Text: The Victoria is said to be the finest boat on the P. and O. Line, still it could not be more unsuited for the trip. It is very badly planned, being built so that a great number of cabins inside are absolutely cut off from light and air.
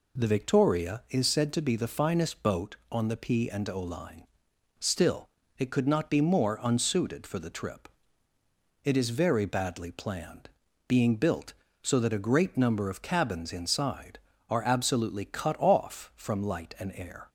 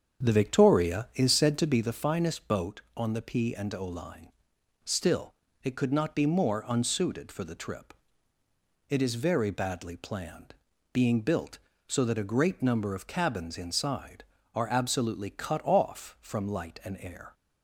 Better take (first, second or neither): first